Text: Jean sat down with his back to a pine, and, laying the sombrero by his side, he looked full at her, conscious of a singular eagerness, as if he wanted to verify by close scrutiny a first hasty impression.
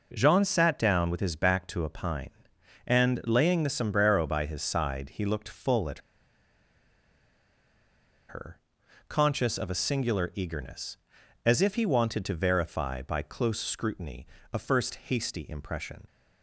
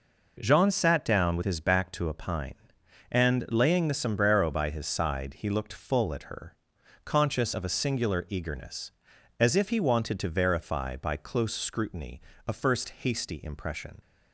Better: second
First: pauses between "at" and "her"; strong; at 5.9 s; 2.2 s long // pauses between "scrutiny" and "a"; slight; at 14.2 s; 0.26 s long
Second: pauses between "scrutiny" and "a"; slight; at 12.2 s; 0.26 s long

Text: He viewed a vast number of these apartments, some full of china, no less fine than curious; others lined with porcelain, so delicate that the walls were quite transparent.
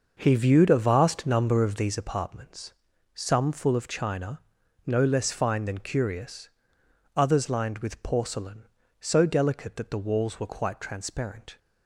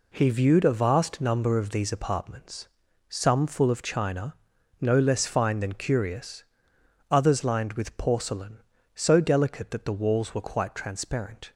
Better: second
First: starts louder than the rest; noticeable; until 2.0 s; 6 dB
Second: none

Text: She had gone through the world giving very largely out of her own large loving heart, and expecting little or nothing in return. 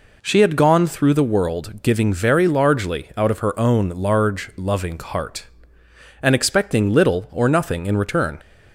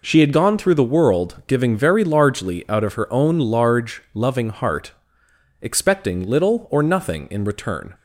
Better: first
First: none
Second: skips "and"; at 5.2 s

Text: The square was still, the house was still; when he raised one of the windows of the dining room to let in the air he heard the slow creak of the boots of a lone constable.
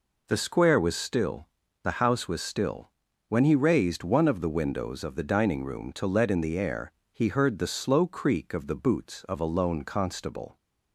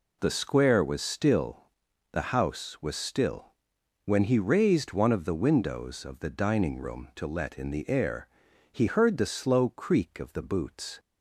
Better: first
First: pauses between "air" and "he"; slight; at 6.9 s; 0.22 s long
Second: pauses between "air" and "he"; at 8.2 s; 0.42 s long // stops before "of a lone constable"; at 10.9 s

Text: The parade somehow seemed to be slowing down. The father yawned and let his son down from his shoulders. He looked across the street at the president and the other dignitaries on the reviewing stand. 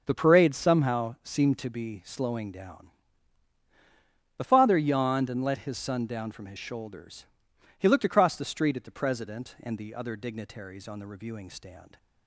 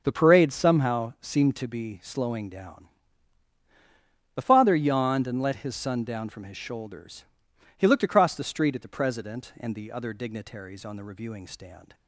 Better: neither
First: starts louder than the rest; until 1.0 s; 6.5 dB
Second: starts louder than the rest; until 1.0 s; 6.5 dB

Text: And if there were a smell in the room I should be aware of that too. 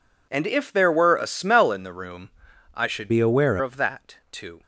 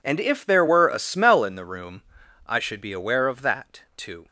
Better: second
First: pauses between "room" and "I"; at 2.2 s; 0.44 s long // changes voice from "be" to "aware"; from 3.0 to 3.5 s; 0.5 s long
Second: pauses between "room" and "I"; at 2.0 s; 0.44 s long

